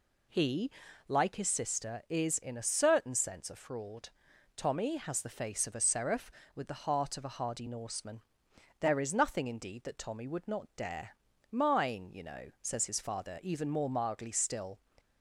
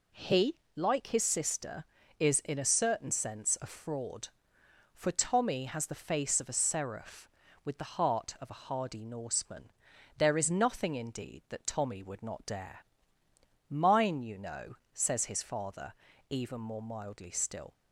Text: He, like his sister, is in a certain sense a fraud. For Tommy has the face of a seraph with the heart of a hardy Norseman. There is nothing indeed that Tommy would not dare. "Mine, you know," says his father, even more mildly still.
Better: second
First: skips "For"; at 4.3 s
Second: none

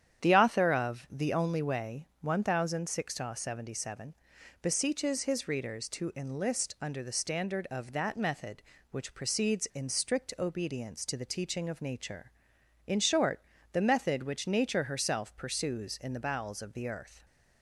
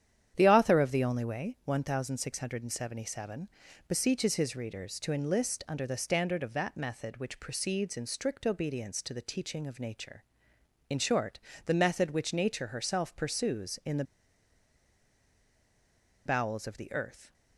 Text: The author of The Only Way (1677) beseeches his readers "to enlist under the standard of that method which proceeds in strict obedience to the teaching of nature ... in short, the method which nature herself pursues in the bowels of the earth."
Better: first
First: starts louder than the rest; strong; until 1.2 s; 9 dB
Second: starts louder than the rest; strong; until 1.3 s; 9.5 dB // pauses between "the" and "bowels"; strong; at 14.0 s; 2.2 s long

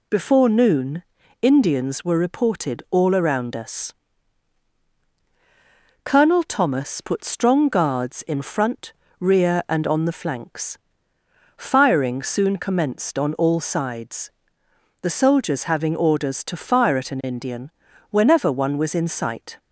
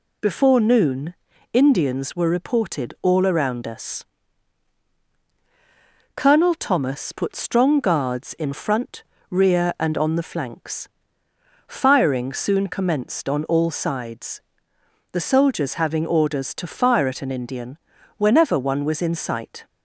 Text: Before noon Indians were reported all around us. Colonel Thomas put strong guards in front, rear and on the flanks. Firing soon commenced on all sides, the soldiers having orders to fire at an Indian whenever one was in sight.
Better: neither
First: pauses between "noon" and "Indians"; at 1.0 s; 0.40 s long // pauses between "Indian" and "whenever"; at 17.7 s; 0.38 s long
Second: pauses between "noon" and "Indians"; at 1.1 s; 0.40 s long // pauses between "Indian" and "whenever"; at 17.7 s; 0.38 s long

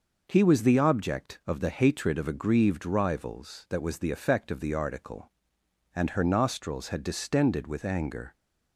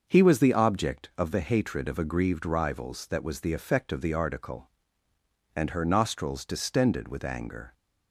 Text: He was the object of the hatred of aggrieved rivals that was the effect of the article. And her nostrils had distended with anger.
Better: first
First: none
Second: starts louder than the rest; until 1.0 s; 6 dB // skips "had"; at 6.4 s

